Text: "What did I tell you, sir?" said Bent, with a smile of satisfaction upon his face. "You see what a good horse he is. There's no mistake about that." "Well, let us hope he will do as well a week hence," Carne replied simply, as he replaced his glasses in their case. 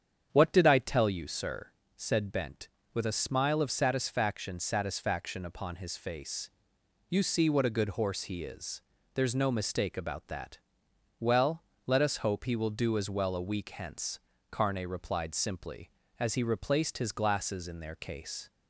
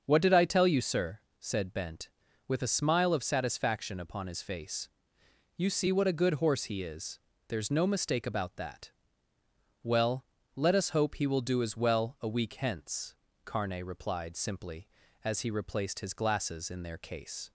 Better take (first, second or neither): second